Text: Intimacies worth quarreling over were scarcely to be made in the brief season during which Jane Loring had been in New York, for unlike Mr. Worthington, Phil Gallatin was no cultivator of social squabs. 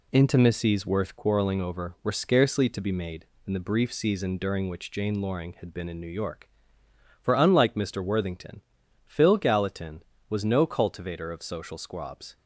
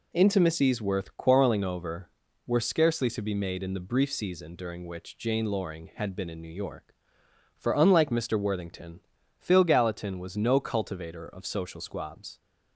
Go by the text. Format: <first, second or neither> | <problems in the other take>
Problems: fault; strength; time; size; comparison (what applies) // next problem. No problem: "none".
neither | none